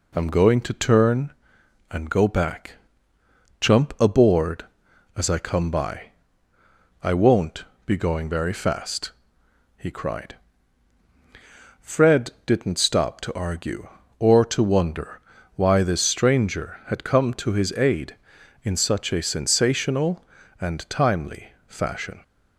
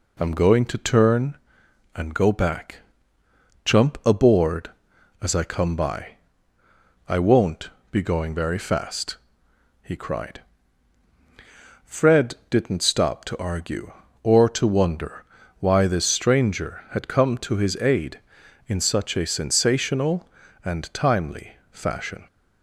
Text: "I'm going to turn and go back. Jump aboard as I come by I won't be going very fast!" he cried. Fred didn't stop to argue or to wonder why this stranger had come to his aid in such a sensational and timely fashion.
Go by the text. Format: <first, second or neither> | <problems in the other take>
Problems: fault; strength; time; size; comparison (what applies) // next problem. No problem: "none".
neither | pauses between "by" and "I"; noticeable; the same in both // pauses between "won't" and "be"; slight; the same in both // pauses between "wonder" and "why"; slight; the same in both